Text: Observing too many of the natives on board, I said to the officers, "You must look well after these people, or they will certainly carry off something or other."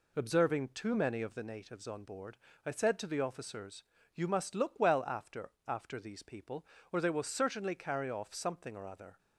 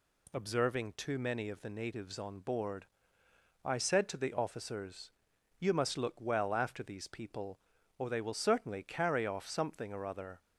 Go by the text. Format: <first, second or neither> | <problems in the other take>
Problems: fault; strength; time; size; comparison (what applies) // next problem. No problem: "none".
second | says "after" twice; at 5.6 s